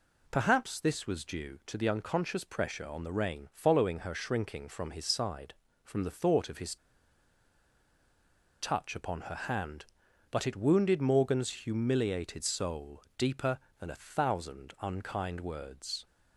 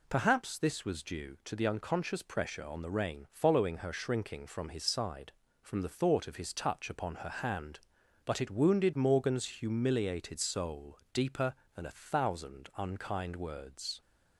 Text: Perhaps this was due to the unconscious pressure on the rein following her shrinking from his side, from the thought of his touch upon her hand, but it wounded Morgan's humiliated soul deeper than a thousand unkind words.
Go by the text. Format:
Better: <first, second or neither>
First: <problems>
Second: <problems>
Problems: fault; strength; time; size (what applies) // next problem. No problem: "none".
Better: second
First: pauses between "his" and "touch"; strong; at 6.7 s; 1.8 s long // pauses between "soul" and "deeper"; slight; at 13.0 s; 0.16 s long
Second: pauses between "soul" and "deeper"; slight; at 10.9 s; 0.16 s long